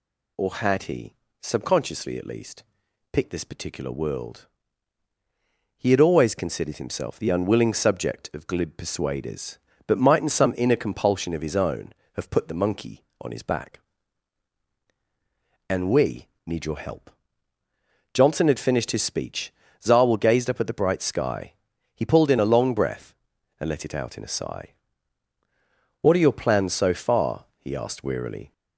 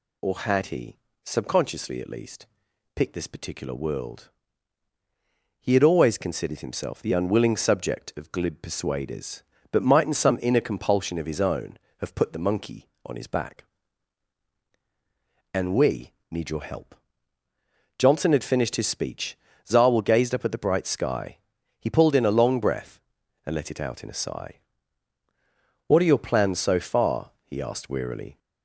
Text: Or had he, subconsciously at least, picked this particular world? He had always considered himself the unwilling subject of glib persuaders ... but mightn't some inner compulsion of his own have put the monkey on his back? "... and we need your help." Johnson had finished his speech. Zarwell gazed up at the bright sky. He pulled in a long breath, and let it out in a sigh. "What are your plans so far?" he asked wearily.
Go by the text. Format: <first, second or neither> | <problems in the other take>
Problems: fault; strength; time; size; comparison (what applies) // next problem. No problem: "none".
neither | pauses between "we" and "need"; slight; the same in both